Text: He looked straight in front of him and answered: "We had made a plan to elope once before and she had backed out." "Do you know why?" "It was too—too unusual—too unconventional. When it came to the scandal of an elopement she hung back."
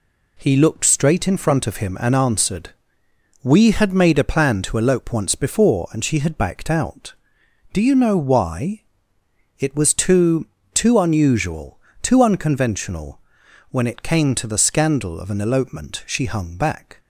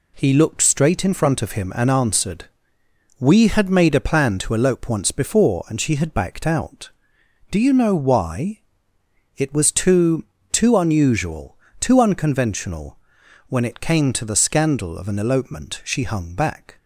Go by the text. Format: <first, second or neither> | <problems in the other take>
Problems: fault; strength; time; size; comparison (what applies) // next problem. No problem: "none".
neither | none